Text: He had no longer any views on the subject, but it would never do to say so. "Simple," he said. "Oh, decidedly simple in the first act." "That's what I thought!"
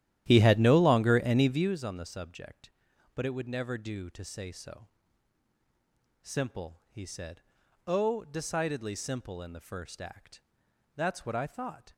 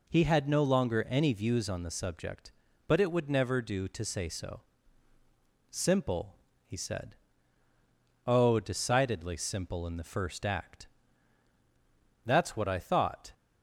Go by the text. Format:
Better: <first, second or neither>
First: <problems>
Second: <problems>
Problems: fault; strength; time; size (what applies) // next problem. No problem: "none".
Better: second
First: starts louder than the rest; strong; until 1.7 s; 12.5 dB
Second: none